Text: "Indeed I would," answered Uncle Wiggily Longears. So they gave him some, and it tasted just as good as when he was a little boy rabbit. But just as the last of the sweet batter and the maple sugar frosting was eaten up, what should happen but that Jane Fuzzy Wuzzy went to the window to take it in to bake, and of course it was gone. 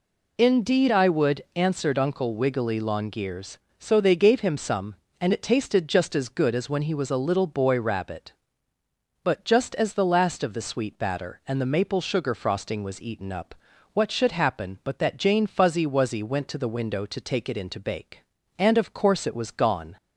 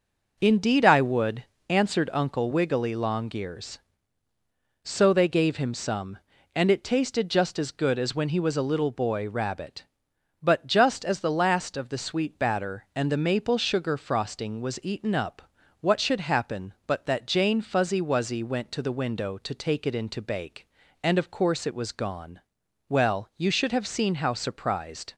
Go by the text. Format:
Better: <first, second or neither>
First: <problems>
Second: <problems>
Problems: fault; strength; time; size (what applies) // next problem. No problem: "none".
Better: first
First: none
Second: goes on to say "Well you should have seen how surprised"; strong; from 22.9 s on; 2.2 s long